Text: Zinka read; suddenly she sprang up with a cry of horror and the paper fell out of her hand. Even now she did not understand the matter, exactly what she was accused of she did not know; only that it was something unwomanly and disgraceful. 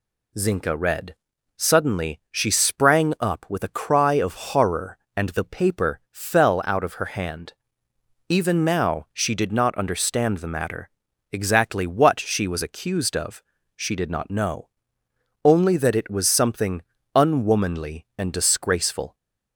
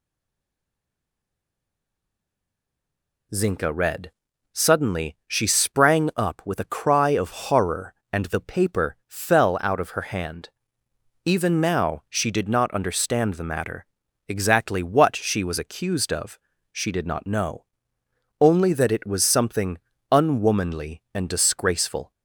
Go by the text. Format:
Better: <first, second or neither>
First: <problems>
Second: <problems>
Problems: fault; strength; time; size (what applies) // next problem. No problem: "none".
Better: first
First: pauses between "of" and "she"; slight; at 13.4 s; 0.32 s long // pauses between "something" and "unwomanly"; slight; at 16.8 s; 0.34 s long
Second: stays silent before the first word; strong; until 3.3 s; 3.3 s long // pauses between "of" and "she"; slight; at 16.3 s; 0.32 s long // pauses between "something" and "unwomanly"; slight; at 19.7 s; 0.34 s long